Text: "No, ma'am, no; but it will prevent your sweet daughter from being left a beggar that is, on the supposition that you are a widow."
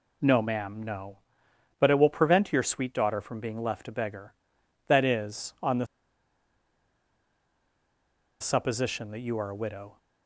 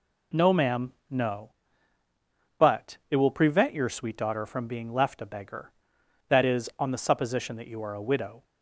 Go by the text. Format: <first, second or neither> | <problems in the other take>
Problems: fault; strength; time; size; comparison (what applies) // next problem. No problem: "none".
second | pauses between "the" and "supposition"; strong; at 5.8 s; 2.5 s long